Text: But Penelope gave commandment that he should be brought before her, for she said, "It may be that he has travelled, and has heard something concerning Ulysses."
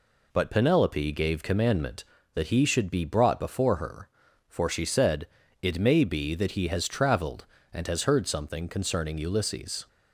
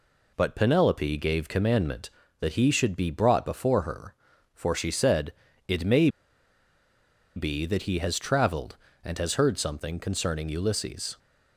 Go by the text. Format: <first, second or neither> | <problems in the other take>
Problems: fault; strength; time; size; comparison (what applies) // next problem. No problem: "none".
first | pauses between "may" and "be"; strong; at 6.0 s; 1.2 s long